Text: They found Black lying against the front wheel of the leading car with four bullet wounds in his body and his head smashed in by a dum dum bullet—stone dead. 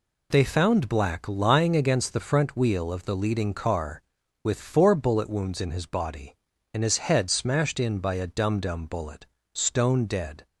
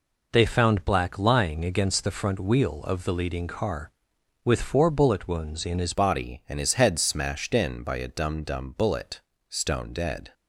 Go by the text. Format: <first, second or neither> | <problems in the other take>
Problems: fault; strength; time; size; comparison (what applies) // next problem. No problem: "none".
first | changes voice at "body"; from 5.9 s on; 4.4 s long